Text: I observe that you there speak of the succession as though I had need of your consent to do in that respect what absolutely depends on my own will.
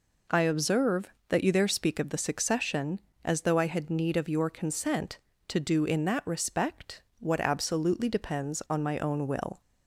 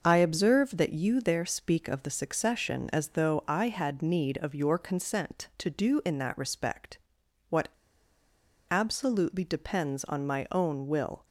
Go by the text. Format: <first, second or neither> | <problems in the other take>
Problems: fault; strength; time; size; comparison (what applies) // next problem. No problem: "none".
first | starts louder than the rest; noticeable; until 1.0 s; 6 dB // pauses between "respect" and "what"; noticeable; at 6.9 s; 0.52 s long; slight in the first // pauses between "what" and "absolutely"; at 7.6 s; 1.0 s long